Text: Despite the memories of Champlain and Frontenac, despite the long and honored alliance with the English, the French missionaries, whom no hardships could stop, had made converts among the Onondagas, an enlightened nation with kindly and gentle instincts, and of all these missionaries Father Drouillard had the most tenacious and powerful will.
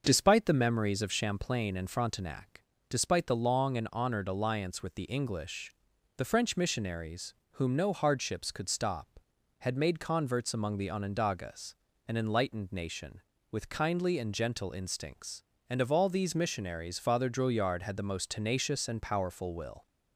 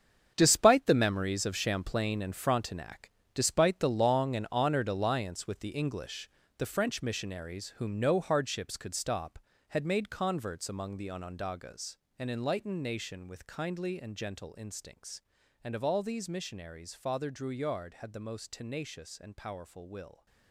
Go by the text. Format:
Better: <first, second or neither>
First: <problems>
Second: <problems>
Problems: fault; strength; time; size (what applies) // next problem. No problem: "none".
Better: first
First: starts louder than the rest; until 1.0 s; 6.5 dB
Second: gets quieter; strong; throughout; 12 dB // starts louder than the rest; strong; until 1.3 s; 7.5 dB